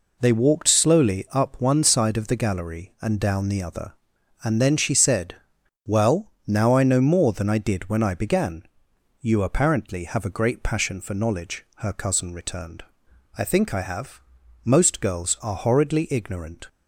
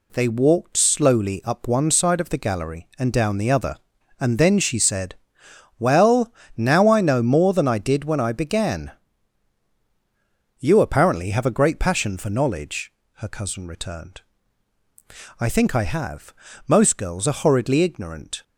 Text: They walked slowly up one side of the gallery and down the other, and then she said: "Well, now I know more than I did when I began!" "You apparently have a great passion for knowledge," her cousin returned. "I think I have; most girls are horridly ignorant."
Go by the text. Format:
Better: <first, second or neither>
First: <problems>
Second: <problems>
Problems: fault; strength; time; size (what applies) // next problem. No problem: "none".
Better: neither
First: none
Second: none